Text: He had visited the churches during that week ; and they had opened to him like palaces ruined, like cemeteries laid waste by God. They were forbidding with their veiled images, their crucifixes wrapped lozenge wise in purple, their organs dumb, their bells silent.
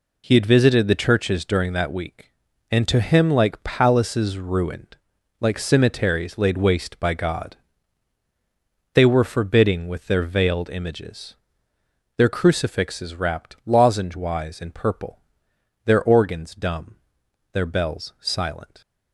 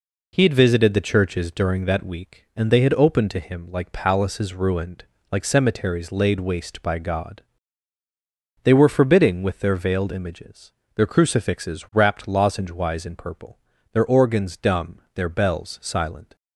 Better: second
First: skips "they had opened"; at 2.8 s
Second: none

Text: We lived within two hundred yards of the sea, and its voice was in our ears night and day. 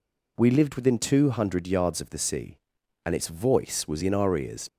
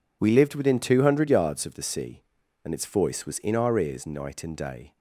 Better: second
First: stops before "night and day"; at 4.6 s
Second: none

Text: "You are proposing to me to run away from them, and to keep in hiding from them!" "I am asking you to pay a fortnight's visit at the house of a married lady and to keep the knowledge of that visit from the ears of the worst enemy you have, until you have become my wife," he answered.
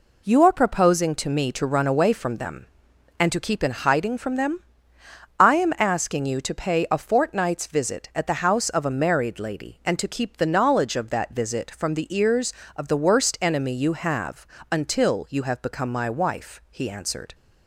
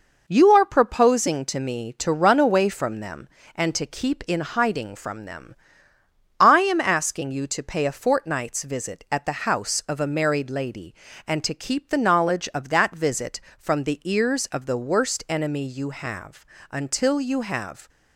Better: first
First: none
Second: stops before "become my wife he answered"; at 17.8 s

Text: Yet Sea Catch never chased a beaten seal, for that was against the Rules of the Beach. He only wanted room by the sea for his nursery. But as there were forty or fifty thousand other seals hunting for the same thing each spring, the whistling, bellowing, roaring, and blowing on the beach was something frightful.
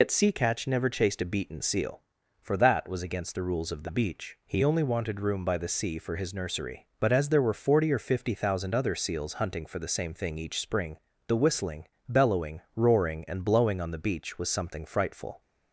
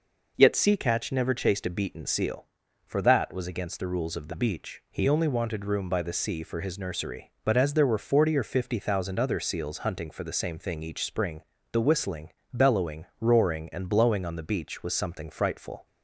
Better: second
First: loses the start of "Yet"; at 0.0 s; 85 ms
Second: none

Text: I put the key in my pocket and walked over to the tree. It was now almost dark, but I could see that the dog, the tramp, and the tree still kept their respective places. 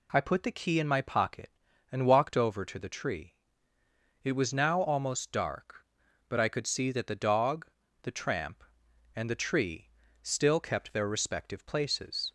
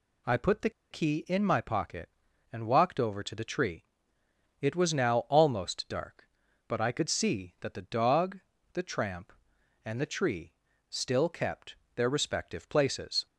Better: first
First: pauses between "tree" and "still"; slight; at 9.9 s; 0.32 s long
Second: pauses between "the" and "key"; slight; at 0.6 s; 0.21 s long // pauses between "tree" and "still"; at 10.5 s; 0.38 s long // pauses between "kept" and "their"; slight; at 11.7 s; 0.20 s long

